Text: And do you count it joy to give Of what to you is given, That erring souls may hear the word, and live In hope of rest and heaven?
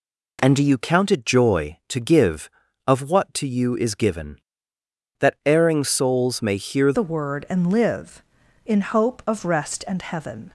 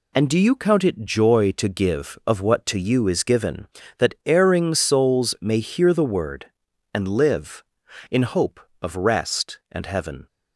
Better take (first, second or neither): second